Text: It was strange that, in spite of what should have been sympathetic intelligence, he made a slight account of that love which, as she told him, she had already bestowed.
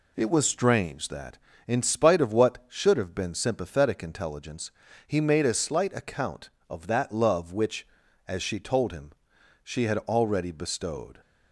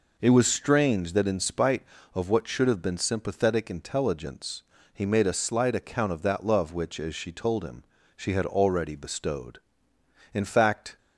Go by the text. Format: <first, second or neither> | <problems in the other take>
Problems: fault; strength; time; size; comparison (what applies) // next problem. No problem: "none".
first | goes on to say "In fact"; noticeable; from 10.3 s on; 0.64 s long